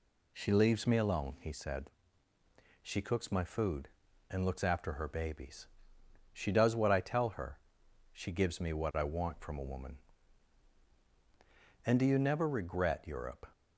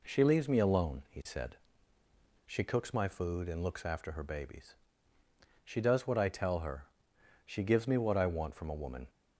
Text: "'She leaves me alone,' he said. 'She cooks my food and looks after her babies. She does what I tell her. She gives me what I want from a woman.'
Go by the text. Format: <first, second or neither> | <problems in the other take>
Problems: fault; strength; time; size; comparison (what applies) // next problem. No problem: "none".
second | goes on to say "And do you never regret Europe"; from 11.8 s on; 1.6 s long